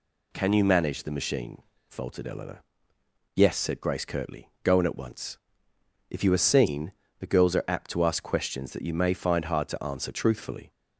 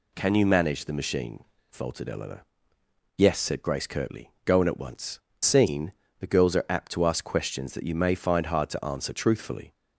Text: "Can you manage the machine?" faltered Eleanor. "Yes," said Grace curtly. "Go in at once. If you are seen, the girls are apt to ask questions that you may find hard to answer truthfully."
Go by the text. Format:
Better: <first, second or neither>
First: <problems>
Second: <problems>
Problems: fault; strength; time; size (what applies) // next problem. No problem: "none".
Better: first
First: none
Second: skips "If you are"; at 5.3 s